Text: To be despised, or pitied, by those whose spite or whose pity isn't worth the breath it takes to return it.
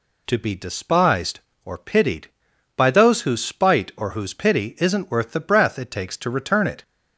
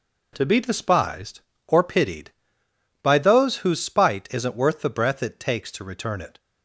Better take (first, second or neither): first